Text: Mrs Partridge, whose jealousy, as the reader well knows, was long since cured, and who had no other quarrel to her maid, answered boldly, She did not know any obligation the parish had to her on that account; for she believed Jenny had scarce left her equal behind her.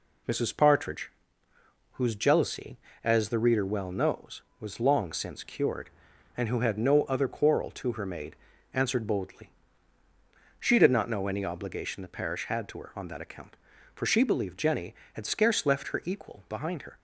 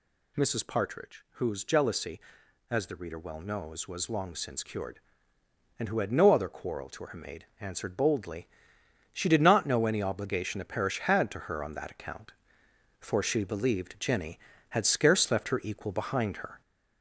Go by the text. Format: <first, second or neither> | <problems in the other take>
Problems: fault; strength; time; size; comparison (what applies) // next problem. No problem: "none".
first | gets louder; throughout; 4 dB